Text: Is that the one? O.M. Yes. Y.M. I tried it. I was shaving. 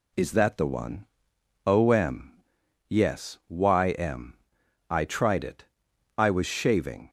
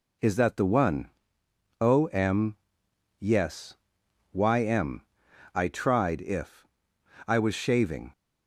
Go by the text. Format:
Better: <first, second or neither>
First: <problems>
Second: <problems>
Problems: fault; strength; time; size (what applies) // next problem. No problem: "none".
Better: first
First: none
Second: says "if" for "it"; at 6.2 s